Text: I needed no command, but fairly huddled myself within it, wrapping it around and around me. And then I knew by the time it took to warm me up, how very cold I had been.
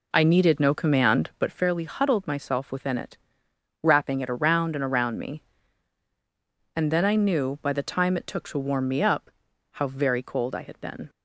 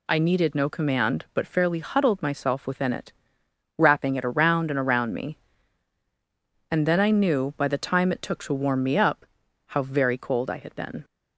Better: second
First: starts louder than the rest; until 1.6 s; 3.5 dB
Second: none

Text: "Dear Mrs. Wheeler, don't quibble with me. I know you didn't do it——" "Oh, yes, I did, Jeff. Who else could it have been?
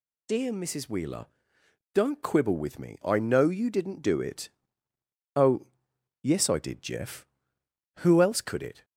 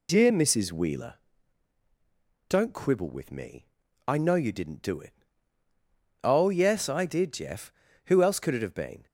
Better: second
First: stops before "have been"; at 8.8 s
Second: none

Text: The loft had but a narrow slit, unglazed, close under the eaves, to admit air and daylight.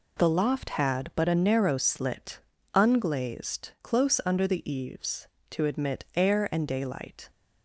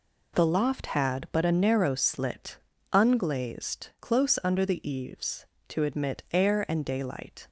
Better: neither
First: none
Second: none

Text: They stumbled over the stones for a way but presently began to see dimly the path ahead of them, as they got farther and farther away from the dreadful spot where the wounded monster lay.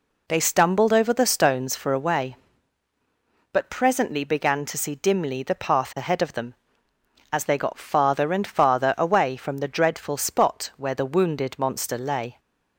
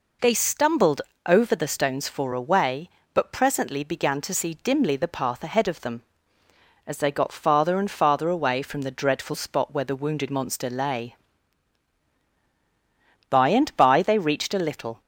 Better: first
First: none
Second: pauses between "stumbled" and "over"; slight; at 1.0 s; 0.24 s long // goes on to say "By and by they reached a little"; strong; from 13.3 s on; 1.7 s long

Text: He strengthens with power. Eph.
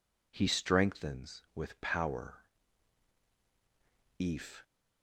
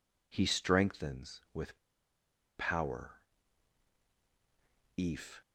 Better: first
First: none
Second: pauses between "with" and "power"; noticeable; at 1.7 s; 0.79 s long

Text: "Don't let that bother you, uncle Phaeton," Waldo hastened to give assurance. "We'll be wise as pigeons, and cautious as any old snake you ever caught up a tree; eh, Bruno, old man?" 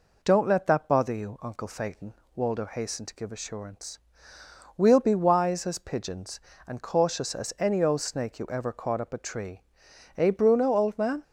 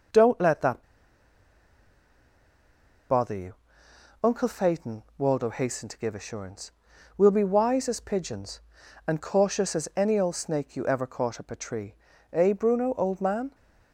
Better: first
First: none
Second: pauses between "that" and "bother"; strong; at 0.8 s; 2.2 s long

